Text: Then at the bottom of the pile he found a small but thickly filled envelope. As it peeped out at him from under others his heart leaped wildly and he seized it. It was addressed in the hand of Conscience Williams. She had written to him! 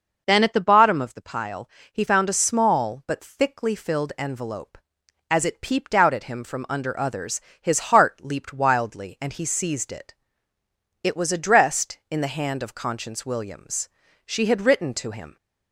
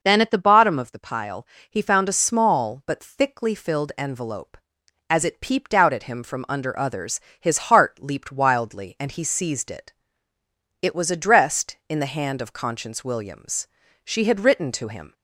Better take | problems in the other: neither | pauses between "pile" and "he"; slight; the same in both // pauses between "others" and "his"; slight; the same in both

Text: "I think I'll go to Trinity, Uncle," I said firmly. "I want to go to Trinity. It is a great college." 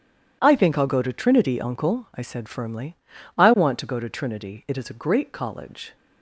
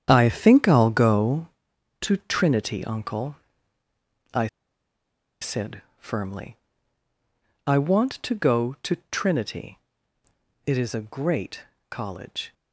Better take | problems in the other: first | starts louder than the rest; strong; until 1.0 s; 9 dB // pauses between "I" and "said"; noticeable; at 4.4 s; 0.94 s long // pauses between "said" and "firmly"; slight; at 5.8 s; 0.16 s long // pauses between "great" and "college"; slight; at 11.6 s; 0.26 s long

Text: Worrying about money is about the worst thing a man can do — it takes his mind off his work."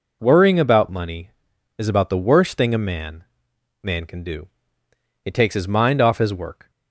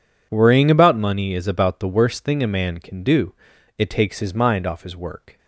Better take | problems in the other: second | says "man" twice; at 3.8 s

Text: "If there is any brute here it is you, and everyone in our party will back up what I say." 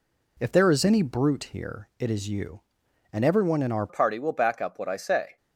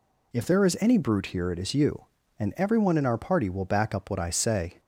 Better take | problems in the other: second | changes voice at "party"; from 3.8 s on; 1.5 s long

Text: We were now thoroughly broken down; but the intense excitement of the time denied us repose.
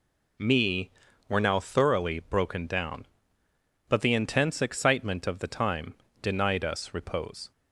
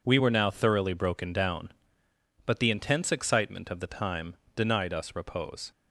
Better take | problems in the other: second | says "Me" for "We"; at 0.3 s // pauses between "time" and "denied"; slight; at 5.9 s; 0.30 s long; slight in the second

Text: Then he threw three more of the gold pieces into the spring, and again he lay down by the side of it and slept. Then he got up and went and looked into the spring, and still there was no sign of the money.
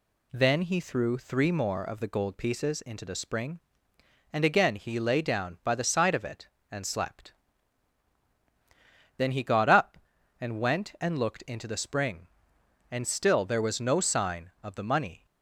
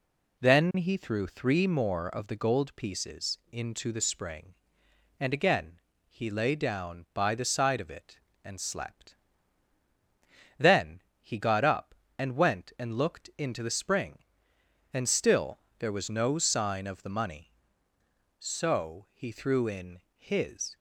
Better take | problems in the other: first | pauses between "again" and "he"; slight; at 5.7 s; 0.30 s long // pauses between "Then" and "he"; slight; at 11.0 s; 0.20 s long // pauses between "still" and "there"; slight; at 15.5 s; 0.20 s long // goes on to say "So he threw in his"; strong; from 18.3 s on; 2.3 s long

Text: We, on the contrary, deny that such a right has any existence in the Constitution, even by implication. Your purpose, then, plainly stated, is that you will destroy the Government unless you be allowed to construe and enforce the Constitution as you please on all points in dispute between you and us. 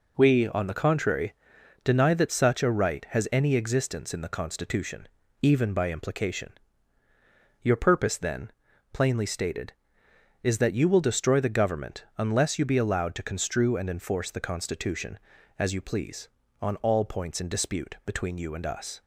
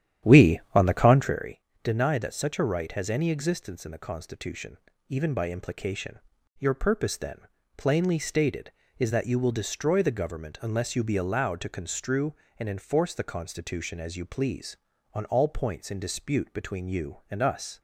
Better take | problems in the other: first | starts louder than the rest; strong; until 1.4 s; 10.5 dB

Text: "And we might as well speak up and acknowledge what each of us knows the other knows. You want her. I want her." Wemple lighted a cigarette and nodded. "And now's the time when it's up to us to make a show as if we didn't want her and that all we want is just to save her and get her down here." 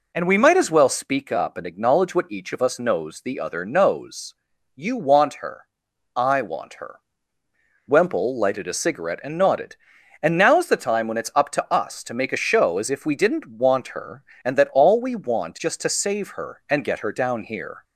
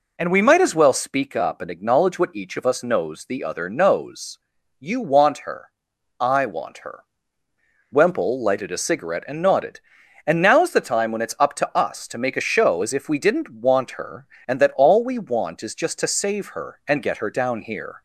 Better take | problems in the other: second | skips "is"; at 15.5 s

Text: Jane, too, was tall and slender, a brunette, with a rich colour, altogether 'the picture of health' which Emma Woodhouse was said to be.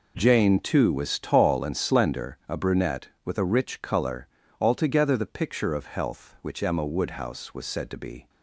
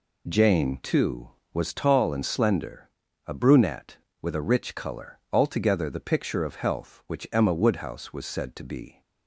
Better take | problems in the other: neither | none

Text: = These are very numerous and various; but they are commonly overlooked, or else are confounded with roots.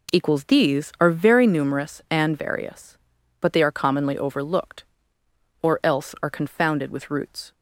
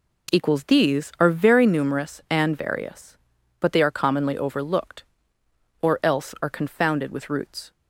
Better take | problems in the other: neither | none

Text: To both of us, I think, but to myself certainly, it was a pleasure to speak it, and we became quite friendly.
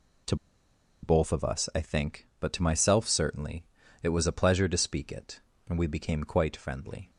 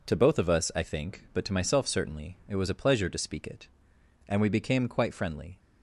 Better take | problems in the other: second | pauses between "To" and "both"; noticeable; at 0.3 s; 0.68 s long

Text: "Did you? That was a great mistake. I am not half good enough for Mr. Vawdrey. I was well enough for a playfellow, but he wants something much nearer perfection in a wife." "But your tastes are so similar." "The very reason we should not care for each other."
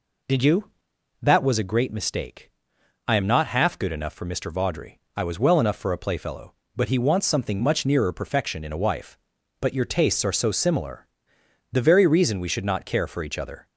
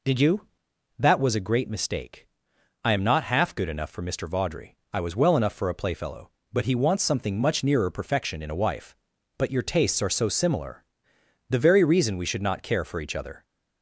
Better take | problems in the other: neither | none

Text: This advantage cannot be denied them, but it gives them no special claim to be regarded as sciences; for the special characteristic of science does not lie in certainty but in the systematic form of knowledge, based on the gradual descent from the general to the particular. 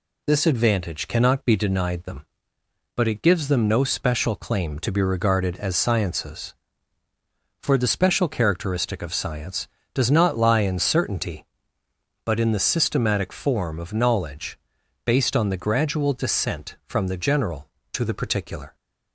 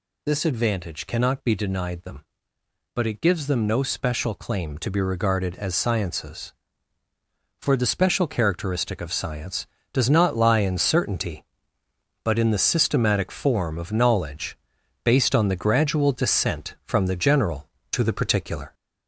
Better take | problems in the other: first | gets louder; throughout; 3.5 dB

